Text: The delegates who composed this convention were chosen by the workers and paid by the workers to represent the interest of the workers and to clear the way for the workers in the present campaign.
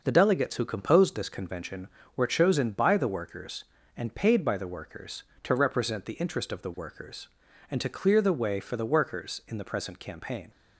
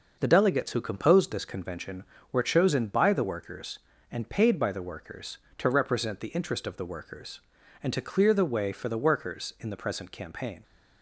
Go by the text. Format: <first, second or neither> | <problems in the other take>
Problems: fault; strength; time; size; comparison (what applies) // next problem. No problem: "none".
neither | none